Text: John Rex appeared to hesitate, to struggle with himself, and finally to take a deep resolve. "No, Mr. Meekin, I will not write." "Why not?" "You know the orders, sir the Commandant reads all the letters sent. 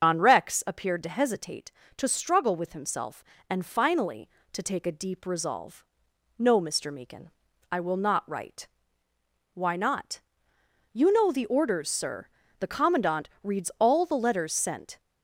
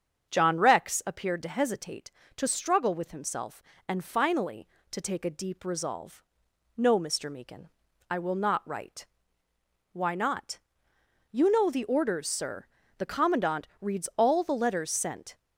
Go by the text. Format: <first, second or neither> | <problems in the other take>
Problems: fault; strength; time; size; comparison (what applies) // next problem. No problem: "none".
second | loses the start of "John"; at 0.0 s; 120 ms // starts louder than the rest; until 1.0 s; 6.5 dB; also in the second // pauses between "sir" and "the"; slight; at 12.2 s; 0.32 s long; slight in the second